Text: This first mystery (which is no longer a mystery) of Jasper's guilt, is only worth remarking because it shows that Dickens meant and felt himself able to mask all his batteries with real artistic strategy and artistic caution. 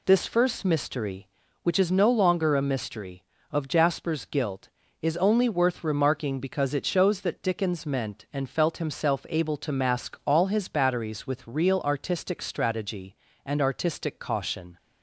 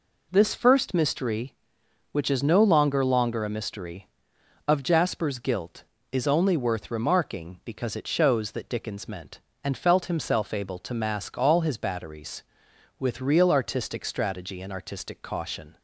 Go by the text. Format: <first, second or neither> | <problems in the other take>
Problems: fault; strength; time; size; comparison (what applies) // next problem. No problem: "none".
first | says "longer" twice; at 3.0 s